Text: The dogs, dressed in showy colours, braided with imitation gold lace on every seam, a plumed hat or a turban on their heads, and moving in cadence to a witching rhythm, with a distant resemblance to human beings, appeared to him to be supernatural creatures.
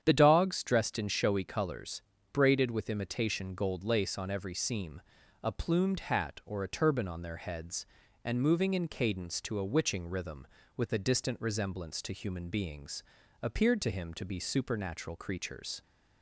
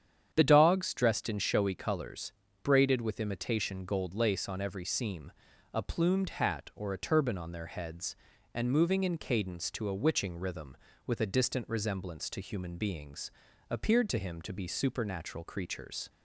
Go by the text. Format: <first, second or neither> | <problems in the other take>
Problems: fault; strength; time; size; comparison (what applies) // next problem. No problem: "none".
neither | starts louder than the rest; strong; the same in both